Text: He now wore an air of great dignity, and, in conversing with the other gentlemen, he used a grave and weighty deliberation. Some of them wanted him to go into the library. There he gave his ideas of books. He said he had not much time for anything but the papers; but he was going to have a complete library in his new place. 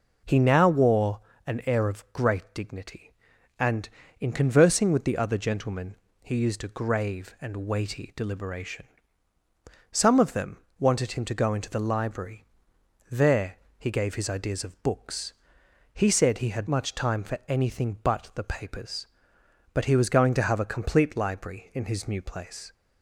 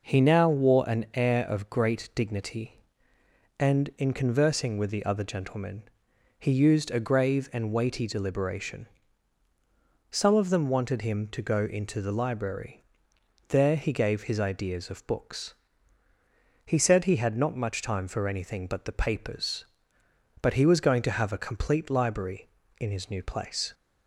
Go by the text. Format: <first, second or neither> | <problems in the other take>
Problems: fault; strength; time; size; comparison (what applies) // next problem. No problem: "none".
second | pauses between "wore" and "an"; slight; at 1.2 s; 0.26 s long // pauses between "them" and "wanted"; slight; at 10.5 s; 0.22 s long // pauses between "There" and "he"; slight; at 13.5 s; 0.22 s long // skips "not"; at 16.6 s